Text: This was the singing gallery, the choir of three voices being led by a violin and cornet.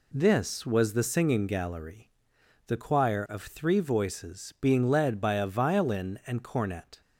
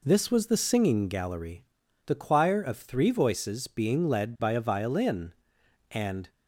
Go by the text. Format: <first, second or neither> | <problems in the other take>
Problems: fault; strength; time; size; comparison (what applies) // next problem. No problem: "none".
first | stops before "cornet"; at 6.2 s